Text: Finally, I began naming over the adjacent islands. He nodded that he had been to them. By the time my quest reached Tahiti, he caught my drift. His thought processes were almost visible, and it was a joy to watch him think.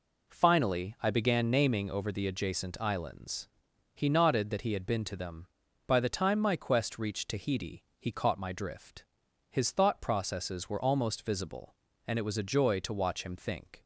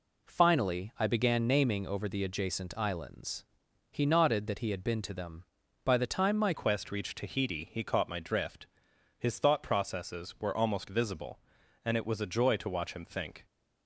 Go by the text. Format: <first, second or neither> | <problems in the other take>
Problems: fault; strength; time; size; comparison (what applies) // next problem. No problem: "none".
first | changes voice at "quest"; from 6.5 s on; 6.9 s long